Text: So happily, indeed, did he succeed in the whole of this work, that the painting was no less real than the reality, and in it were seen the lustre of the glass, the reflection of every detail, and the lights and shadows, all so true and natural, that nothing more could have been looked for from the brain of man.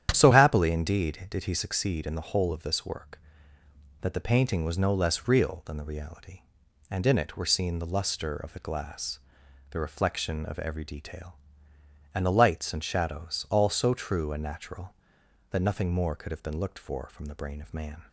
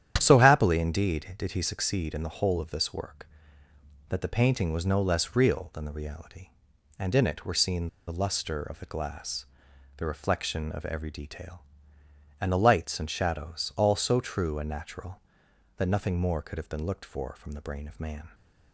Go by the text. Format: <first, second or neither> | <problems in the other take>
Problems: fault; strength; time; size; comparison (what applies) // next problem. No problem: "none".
first | starts louder than the rest; strong; until 1.1 s; 10 dB; strong in the first // pauses between "seen" and "the"; slight; at 7.8 s; 0.20 s long